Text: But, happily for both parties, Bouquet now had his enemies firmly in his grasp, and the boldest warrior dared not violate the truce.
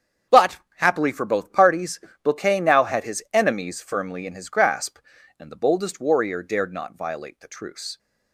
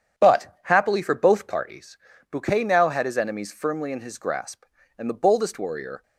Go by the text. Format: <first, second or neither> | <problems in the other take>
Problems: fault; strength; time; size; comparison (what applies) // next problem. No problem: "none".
first | starts louder than the rest; strong; until 1.2 s; 8 dB; strong in the first // stops before "dared not violate the truce"; at 6.0 s